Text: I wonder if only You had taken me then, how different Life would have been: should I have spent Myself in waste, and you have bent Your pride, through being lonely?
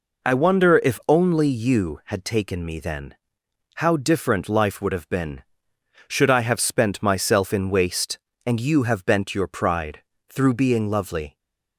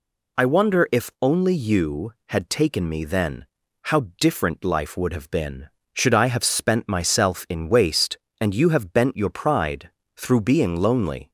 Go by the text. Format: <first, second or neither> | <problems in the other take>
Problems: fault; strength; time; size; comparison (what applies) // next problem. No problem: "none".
second | says "lovely" for "lonely"; at 10.8 s